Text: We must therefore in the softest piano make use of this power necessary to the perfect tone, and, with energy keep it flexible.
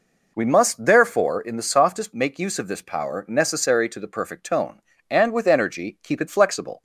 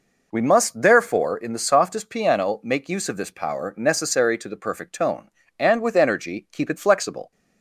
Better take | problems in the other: second | skips "piano"; at 2.1 s

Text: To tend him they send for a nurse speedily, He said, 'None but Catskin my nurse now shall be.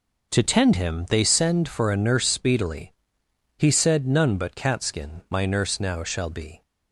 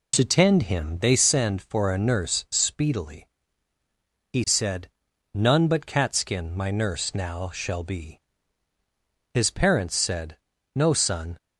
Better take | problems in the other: first | goes on to say "His parents said No son"; strong; from 9.3 s on; 2.0 s long

